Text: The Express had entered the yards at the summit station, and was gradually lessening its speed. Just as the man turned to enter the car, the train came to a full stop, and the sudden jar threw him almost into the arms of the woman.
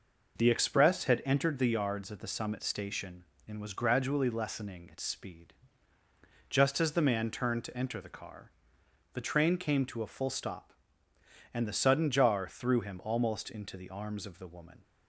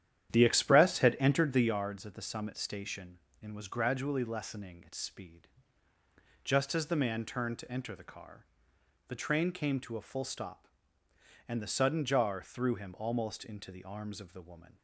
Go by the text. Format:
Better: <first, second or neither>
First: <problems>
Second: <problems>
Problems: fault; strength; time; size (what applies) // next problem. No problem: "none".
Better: first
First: none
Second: starts louder than the rest; strong; until 1.9 s; 10.5 dB